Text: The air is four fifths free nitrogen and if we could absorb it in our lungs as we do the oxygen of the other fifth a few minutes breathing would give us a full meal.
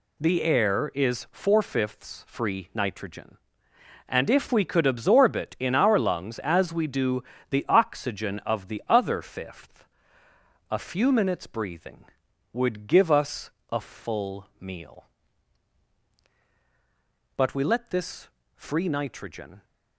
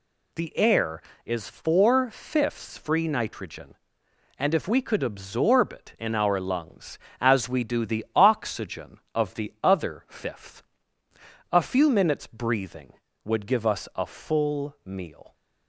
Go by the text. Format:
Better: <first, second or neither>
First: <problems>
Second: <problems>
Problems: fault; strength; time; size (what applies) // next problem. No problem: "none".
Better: second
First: pauses between "do" and "the"; slight; at 7.2 s; 0.24 s long // pauses between "fifth" and "a"; noticeable; at 9.8 s; 0.84 s long // pauses between "us" and "a"; slight; at 13.5 s; 0.22 s long // goes on to say "But we let this free nitrogen"; strong; from 17.3 s on; 2.2 s long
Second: pauses between "fifth" and "a"; noticeable; at 10.6 s; 0.90 s long